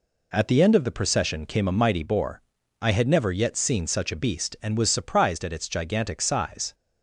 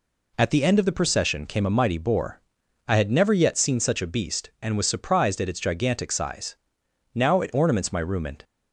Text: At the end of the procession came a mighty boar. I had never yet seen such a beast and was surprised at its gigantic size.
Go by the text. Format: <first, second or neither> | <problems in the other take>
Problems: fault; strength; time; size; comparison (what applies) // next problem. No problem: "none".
first | goes on to say "Now it ornaments my room and"; noticeable; from 7.1 s on; 1.3 s long